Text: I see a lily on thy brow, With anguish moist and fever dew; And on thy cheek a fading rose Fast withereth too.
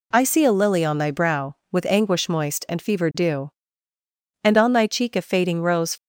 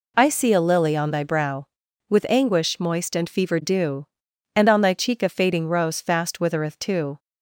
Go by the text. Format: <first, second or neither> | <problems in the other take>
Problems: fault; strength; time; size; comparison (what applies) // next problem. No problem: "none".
second | stops before "Fast withereth too"; at 5.9 s